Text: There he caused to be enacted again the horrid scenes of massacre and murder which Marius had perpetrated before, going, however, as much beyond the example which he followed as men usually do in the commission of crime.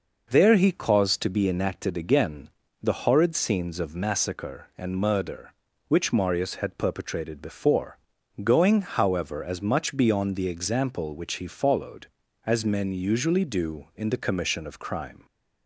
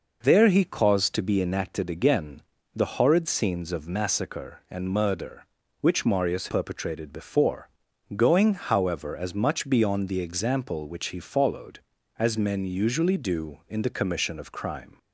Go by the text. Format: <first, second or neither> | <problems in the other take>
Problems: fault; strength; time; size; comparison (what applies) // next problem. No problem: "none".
first | pauses between "again" and "the"; slight; at 2.4 s; 0.32 s long; slight in the first // skips "had"; at 6.4 s